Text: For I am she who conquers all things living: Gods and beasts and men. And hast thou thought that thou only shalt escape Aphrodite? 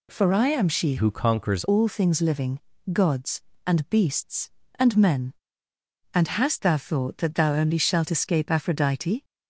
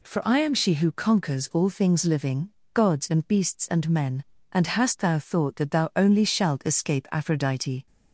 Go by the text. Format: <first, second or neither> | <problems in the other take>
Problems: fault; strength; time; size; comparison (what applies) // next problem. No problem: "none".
second | changes voice from "who" to "conquers"; from 0.9 to 1.6 s; 0.7 s long